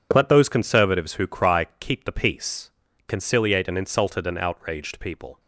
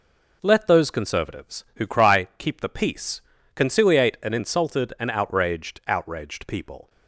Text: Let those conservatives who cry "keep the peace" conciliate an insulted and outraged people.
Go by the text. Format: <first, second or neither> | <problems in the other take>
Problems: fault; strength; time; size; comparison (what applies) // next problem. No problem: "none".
first | pauses between "peace" and "conciliate"; slight; at 3.1 s; 0.36 s long; also in the first // says "outraged" twice; at 5.8 s